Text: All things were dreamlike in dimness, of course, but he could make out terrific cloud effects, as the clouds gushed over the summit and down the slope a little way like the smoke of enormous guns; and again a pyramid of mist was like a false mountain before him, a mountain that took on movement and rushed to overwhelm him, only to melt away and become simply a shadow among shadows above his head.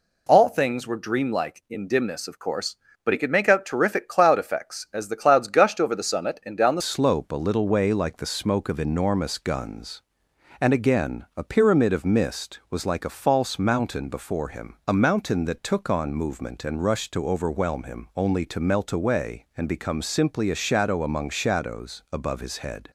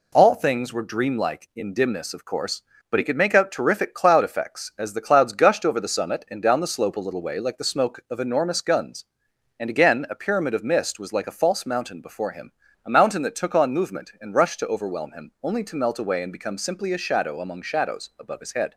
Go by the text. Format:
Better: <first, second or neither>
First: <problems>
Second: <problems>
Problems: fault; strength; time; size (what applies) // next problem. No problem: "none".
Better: second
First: changes voice at "slope"; from 6.8 s on; 16.1 s long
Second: none